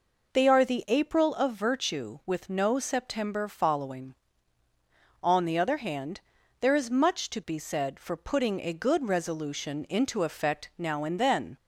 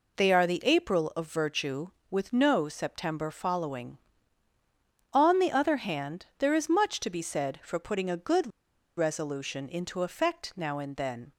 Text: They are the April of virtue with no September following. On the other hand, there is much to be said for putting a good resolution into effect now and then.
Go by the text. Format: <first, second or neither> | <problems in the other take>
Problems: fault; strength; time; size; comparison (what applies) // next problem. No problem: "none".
first | pauses between "good" and "resolution"; noticeable; at 8.4 s; 0.48 s long